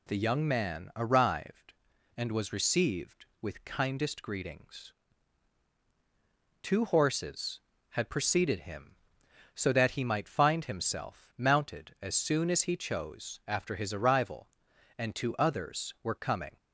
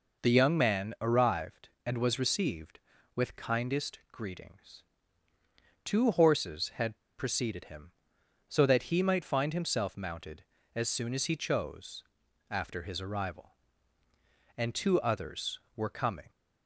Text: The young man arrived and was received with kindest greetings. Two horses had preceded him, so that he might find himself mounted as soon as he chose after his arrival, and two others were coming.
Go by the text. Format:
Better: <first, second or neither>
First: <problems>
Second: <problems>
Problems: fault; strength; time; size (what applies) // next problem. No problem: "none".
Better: first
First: none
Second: pauses between "had" and "preceded"; slight; at 6.9 s; 0.21 s long // pauses between "chose" and "after"; noticeable; at 12.0 s; 0.46 s long